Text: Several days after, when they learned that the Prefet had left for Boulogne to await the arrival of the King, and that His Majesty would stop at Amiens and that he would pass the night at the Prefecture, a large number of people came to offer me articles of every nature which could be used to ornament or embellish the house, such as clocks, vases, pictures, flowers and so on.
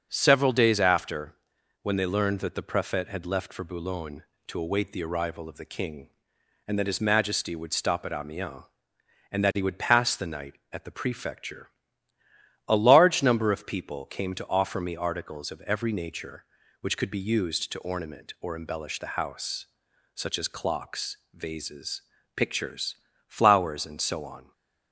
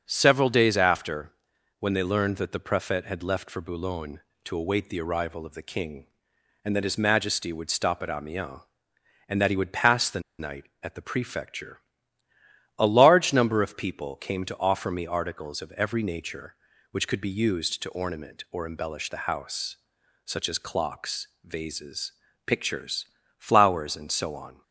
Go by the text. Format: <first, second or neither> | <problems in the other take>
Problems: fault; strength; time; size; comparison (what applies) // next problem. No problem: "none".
first | starts louder than the rest; until 1.0 s; 6.5 dB; also in the first // pauses between "the" and "night"; slight; at 10.1 s; 0.19 s long